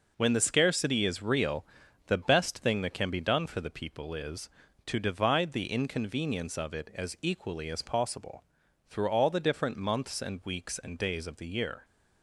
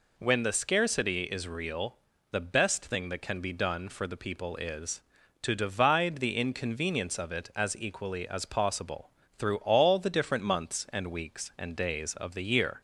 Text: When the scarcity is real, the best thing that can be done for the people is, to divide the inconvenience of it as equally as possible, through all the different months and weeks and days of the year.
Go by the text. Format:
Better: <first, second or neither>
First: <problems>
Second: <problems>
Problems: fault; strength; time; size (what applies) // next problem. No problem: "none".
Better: neither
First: none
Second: none